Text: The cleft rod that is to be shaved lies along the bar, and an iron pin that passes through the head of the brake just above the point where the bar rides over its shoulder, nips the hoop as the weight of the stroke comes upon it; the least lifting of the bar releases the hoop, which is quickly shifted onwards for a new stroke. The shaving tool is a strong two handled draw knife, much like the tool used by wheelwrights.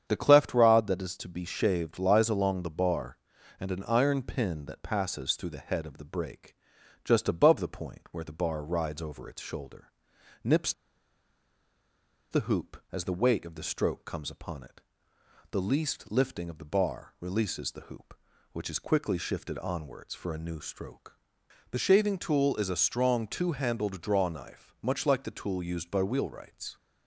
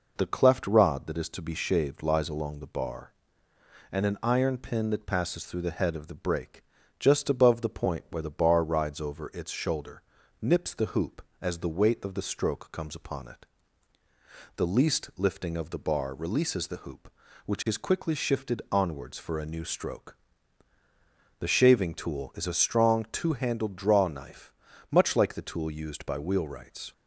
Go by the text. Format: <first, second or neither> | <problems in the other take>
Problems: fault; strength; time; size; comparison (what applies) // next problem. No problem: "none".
second | starts louder than the rest; strong; until 1.0 s; 8.5 dB // pauses between "brake" and "just"; noticeable; at 6.5 s; 0.50 s long; slight in the second // pauses between "nips" and "the"; strong; at 10.7 s; 1.5 s long